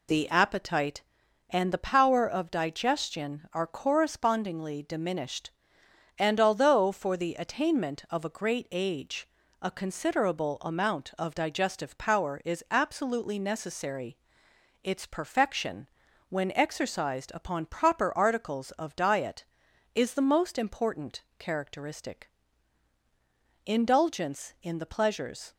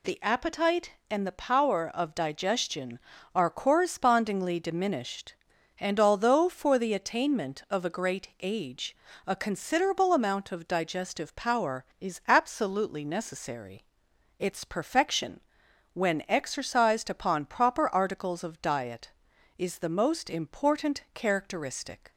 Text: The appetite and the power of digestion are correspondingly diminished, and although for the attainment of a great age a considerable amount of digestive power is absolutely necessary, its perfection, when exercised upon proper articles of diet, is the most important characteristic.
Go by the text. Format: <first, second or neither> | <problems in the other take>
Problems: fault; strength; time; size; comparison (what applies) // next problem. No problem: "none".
second | pauses between "age" and "a"; slight; at 9.2 s; 0.34 s long; slight in the second // pauses between "important" and "characteristic"; slight; at 21.2 s; 0.16 s long // goes on to say "Indulgence in the pleasures"; strong; from 23.6 s on; 1.9 s long